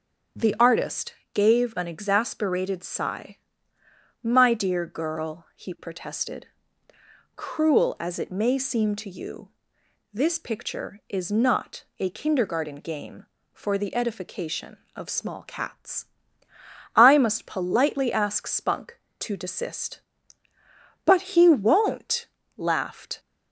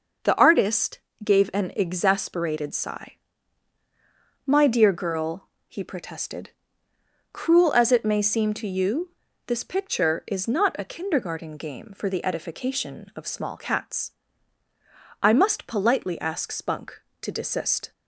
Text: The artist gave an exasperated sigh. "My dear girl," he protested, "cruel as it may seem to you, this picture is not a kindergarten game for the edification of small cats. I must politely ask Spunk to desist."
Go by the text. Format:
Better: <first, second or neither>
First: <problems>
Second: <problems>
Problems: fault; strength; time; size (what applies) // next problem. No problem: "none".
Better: second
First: starts louder than the rest; strong; until 1.5 s; 7.5 dB // pauses between "artist" and "gave"; slight; at 1.1 s; 0.18 s long // goes on to say "But he won't laughed"; strong; from 21.0 s on; 2.1 s long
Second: pauses between "artist" and "gave"; slight; at 0.9 s; 0.24 s long